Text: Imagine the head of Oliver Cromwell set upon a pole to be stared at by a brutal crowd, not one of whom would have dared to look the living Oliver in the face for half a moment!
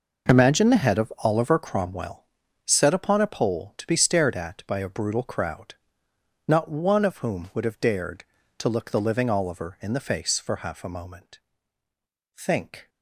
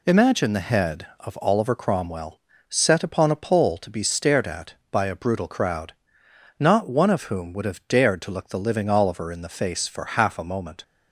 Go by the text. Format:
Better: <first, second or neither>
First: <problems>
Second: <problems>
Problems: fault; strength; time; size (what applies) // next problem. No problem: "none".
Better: second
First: pauses between "Cromwell" and "set"; at 2.2 s; 0.40 s long // goes on to say "Think"; from 12.3 s on; 0.52 s long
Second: pauses between "Cromwell" and "set"; slight; at 2.4 s; 0.28 s long